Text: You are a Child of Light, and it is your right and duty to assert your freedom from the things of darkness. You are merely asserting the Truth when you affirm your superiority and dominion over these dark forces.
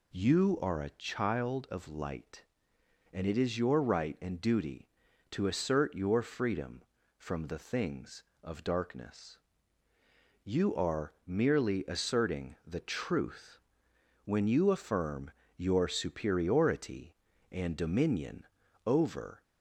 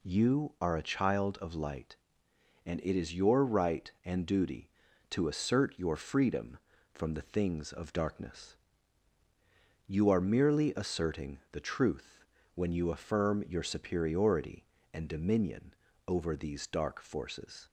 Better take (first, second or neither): second